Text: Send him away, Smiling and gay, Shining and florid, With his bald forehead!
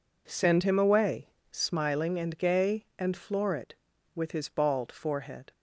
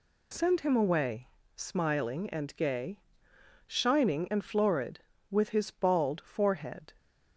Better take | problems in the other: second | skips "Shining"; at 2.9 s

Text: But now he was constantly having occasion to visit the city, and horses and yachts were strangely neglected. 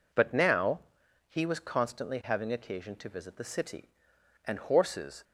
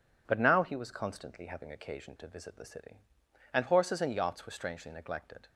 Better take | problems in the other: second | pauses between "now" and "he"; noticeable; at 0.7 s; 0.48 s long // stops before "and yachts were strangely neglected"; at 5.2 s

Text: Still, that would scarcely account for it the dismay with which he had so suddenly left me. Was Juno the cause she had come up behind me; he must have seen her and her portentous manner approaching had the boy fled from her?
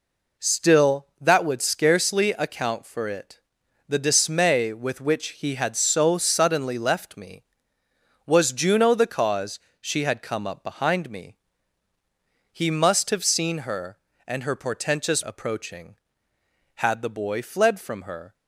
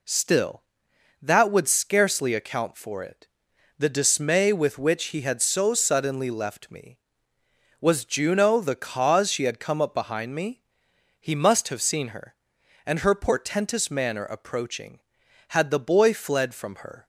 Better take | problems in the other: second | pauses between "it" and "the"; noticeable; at 3.3 s; 0.48 s long; noticeable in the second // pauses between "cause" and "she"; slight; at 9.5 s; 0.20 s long // skips "manner"; at 15.2 s

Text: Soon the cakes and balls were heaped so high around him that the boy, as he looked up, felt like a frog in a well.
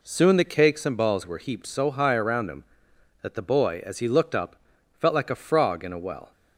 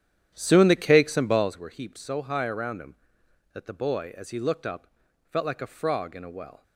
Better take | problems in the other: first | starts louder than the rest; strong; until 1.5 s; 10 dB

